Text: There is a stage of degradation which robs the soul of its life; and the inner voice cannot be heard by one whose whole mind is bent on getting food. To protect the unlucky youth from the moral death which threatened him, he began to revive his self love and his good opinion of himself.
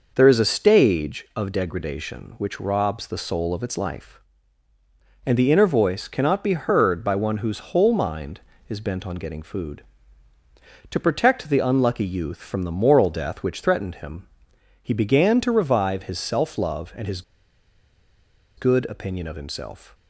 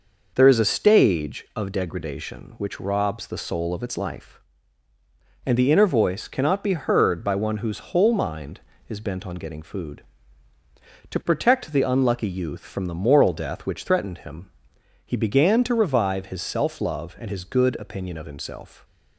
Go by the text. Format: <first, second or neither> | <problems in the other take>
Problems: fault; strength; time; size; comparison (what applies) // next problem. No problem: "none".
second | pauses between "his" and "good"; strong; at 17.2 s; 1.3 s long